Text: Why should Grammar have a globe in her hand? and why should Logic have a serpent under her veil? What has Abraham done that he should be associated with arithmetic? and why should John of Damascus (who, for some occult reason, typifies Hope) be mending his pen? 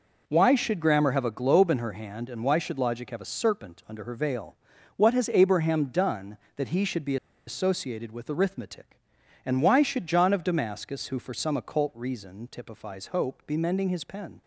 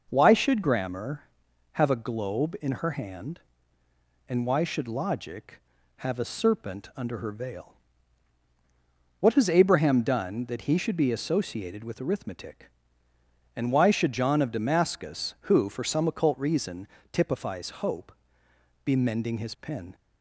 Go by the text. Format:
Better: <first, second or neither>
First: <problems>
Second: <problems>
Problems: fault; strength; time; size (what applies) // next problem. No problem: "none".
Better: second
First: pauses between "be" and "associated"; slight; at 7.1 s; 0.31 s long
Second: none